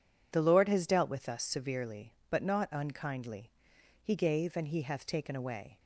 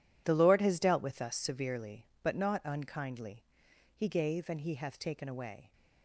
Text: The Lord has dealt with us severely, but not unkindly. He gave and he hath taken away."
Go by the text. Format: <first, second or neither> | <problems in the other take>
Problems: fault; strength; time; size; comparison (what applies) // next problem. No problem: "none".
first | gets quieter; strong; throughout; 13.5 dB